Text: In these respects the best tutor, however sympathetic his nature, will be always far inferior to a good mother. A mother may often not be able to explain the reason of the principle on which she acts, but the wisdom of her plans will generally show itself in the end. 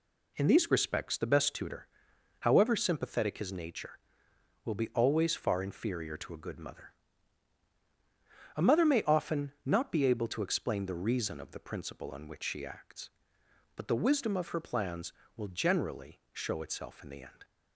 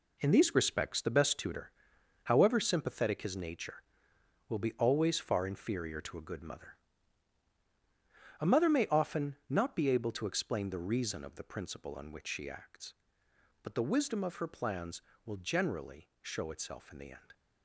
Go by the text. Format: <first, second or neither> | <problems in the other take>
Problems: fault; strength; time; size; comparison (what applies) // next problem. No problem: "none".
first | gets quieter; strong; throughout; 9.5 dB